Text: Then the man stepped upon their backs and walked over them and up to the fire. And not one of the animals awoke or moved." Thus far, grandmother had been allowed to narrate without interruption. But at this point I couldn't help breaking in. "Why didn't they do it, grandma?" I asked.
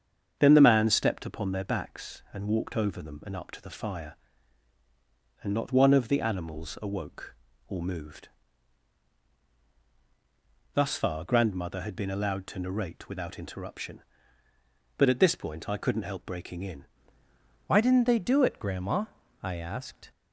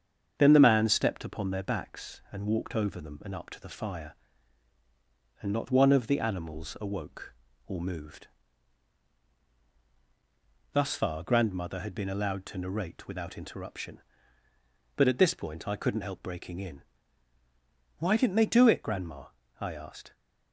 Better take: second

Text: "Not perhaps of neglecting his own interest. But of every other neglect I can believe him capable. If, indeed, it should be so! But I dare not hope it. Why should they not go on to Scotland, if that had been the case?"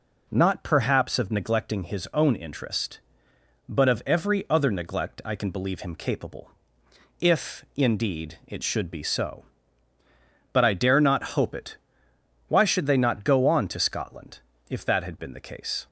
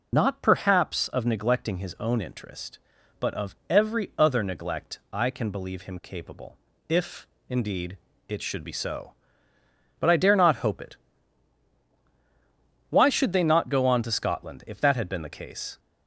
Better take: first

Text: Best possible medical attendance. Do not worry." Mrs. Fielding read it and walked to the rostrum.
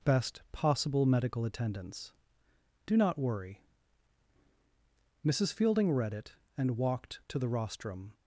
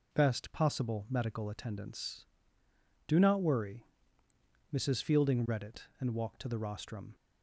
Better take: neither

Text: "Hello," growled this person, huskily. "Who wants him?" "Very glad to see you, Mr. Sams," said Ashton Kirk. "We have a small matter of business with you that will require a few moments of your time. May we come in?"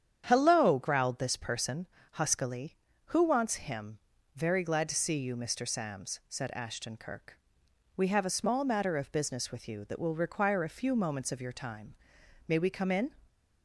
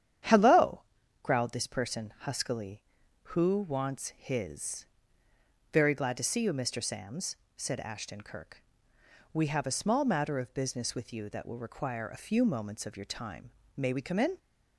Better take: first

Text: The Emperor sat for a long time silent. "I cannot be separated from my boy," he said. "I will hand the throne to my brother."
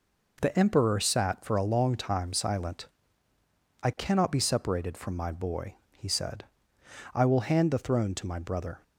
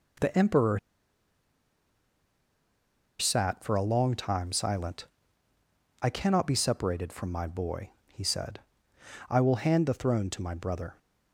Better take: first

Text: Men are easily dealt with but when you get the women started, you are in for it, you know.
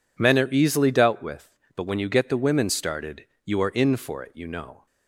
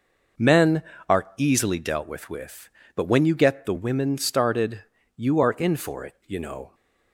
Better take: first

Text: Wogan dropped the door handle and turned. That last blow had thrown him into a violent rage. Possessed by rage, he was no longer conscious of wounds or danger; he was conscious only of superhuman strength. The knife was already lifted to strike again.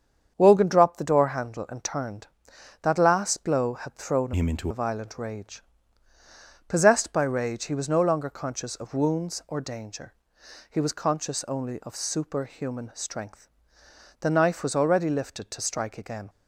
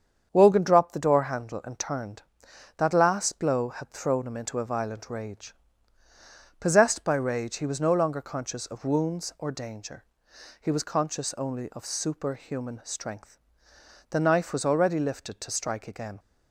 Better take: second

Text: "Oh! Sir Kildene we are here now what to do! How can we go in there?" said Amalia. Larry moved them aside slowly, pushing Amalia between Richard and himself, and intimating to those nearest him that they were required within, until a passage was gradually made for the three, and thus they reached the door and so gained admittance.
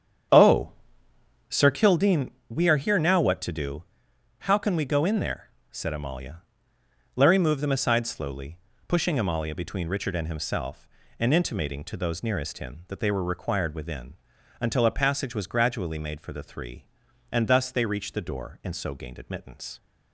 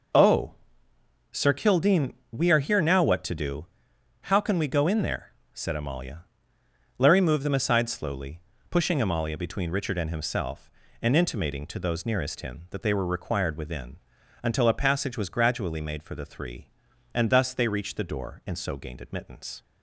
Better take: second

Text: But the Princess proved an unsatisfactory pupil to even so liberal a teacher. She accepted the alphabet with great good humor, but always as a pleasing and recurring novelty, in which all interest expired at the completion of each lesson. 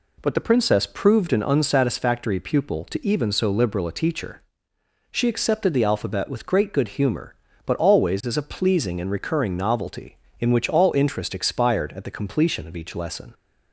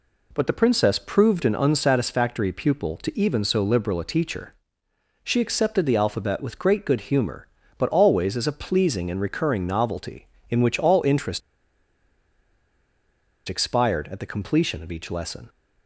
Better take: first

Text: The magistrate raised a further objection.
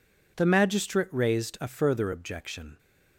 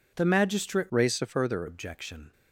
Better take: first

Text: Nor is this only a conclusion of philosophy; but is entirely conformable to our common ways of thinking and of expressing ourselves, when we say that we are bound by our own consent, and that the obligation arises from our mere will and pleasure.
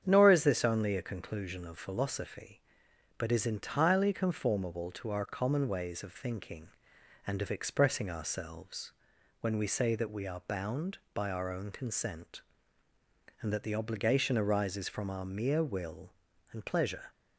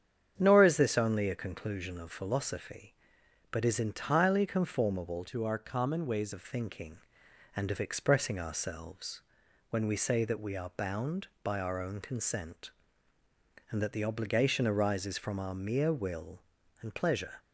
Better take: first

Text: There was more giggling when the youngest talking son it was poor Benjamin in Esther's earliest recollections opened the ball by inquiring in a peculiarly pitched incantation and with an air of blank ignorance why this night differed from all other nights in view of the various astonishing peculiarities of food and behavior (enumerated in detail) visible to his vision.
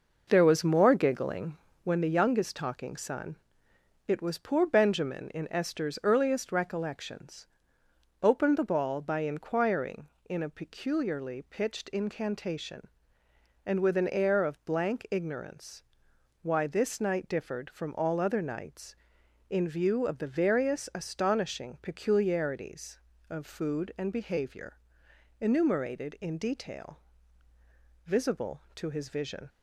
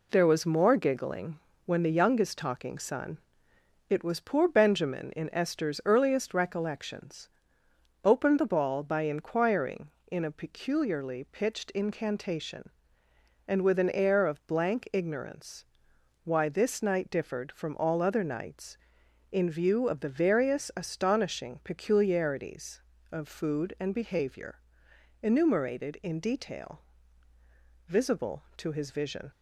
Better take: second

